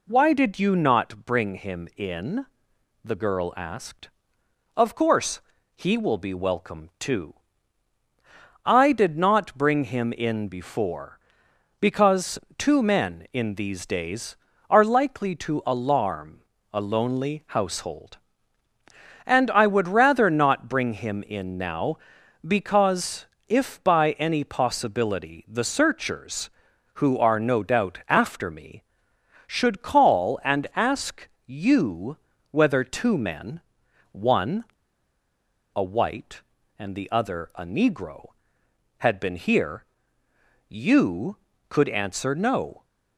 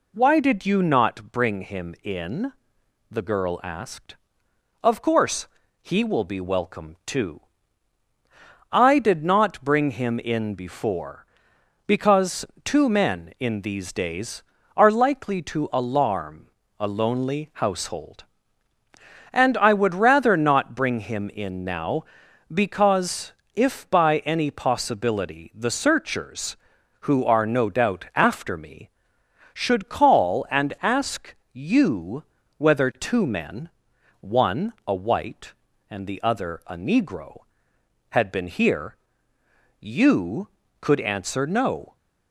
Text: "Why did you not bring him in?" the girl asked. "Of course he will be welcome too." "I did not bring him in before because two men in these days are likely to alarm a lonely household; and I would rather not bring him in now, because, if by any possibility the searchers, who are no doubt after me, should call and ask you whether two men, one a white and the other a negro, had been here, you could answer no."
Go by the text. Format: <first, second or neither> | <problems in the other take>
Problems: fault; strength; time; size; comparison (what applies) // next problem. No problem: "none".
second | pauses between "course" and "he"; slight; at 5.4 s; 0.34 s long; slight in the second // pauses between "because" and "two"; slight; at 12.3 s; 0.18 s long; slight in the second // pauses between "alarm" and "a"; slight; at 16.4 s; 0.30 s long; slight in the second // pauses between "ask" and "you"; slight; at 31.2 s; 0.16 s long; slight in the second // pauses between "you" and "whether"; slight; at 32.1 s; 0.34 s long; slight in the second // pauses between "one" and "a"; at 34.6 s; 1.0 s long